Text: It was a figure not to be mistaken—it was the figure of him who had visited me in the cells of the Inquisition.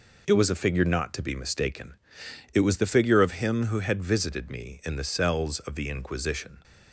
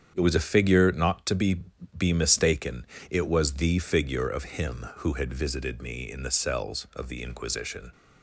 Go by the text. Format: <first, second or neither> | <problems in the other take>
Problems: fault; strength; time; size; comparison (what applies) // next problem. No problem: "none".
first | starts louder than the rest; strong; until 1.1 s; 8 dB // says "be" twice; at 1.9 s